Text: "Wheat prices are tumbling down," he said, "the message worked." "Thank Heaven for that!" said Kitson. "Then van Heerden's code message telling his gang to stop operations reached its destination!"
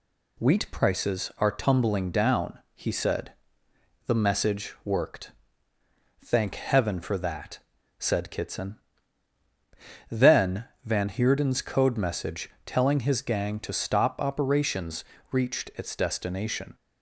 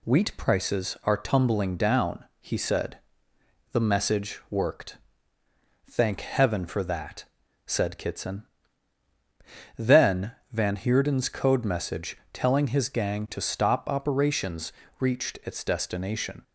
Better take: neither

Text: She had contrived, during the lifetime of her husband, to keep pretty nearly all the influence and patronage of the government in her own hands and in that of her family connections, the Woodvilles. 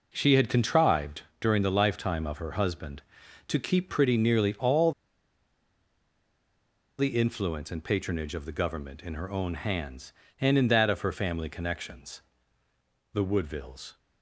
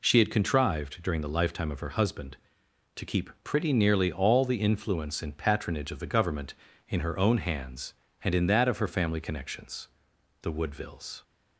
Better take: second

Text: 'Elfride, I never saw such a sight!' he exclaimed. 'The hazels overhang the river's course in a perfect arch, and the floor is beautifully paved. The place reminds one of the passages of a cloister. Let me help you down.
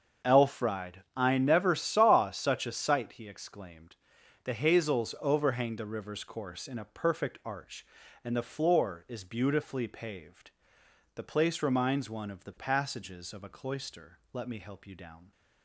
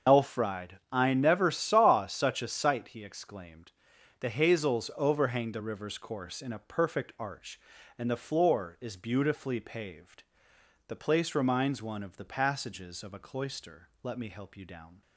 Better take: first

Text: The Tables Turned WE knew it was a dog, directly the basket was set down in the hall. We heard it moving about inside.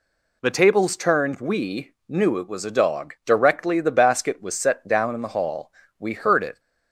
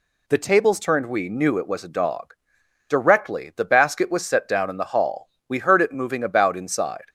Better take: second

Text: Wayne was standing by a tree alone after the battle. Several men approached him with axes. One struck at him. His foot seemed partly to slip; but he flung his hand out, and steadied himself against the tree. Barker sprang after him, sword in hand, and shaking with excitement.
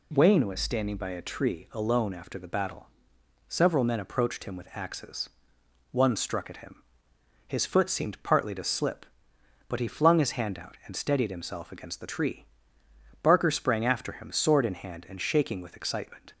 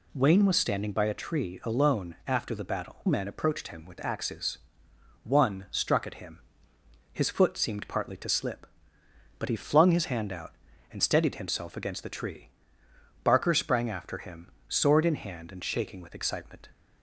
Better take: first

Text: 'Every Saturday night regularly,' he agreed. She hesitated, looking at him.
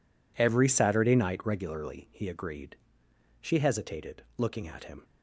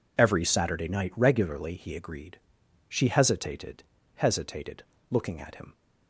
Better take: first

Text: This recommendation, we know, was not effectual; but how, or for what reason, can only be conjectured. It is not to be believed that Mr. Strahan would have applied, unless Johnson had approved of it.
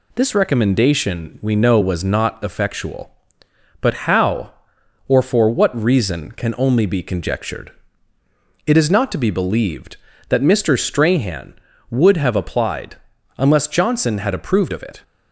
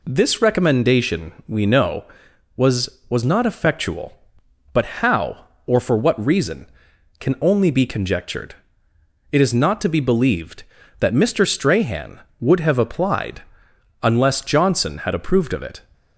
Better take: first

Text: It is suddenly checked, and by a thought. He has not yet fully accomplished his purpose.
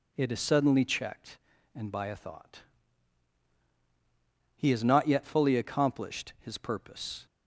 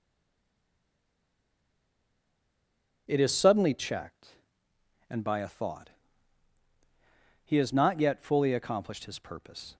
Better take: first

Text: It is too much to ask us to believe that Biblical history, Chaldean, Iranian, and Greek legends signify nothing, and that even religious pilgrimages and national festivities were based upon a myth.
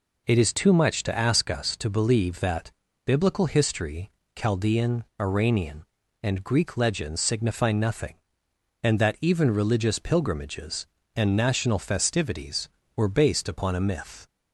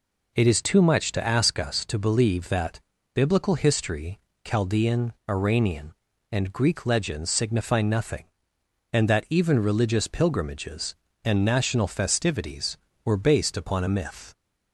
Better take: neither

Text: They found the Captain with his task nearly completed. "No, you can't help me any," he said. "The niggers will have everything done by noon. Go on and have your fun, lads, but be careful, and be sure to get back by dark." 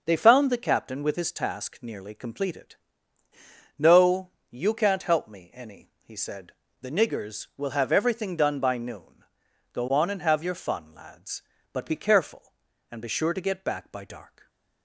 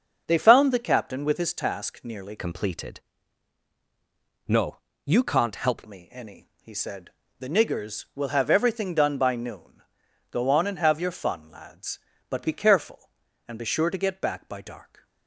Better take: first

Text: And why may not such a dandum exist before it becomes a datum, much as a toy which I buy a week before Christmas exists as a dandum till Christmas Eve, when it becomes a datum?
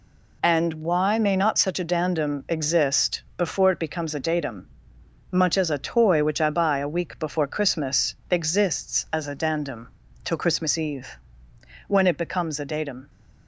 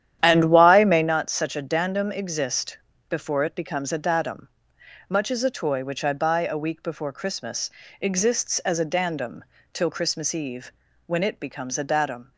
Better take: first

